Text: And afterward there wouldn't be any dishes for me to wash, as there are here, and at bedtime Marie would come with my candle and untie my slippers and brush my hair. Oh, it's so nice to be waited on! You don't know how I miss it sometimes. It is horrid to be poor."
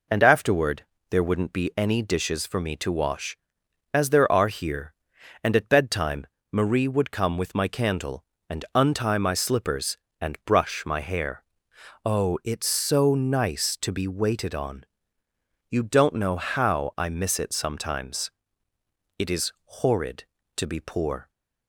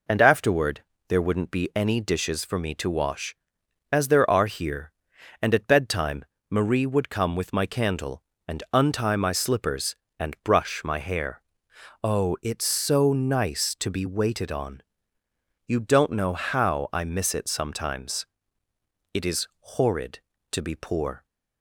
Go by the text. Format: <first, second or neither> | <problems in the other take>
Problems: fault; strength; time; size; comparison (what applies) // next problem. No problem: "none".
neither | pauses between "afterward" and "there"; slight; the same in both // pauses between "bedtime" and "Marie"; slight; the same in both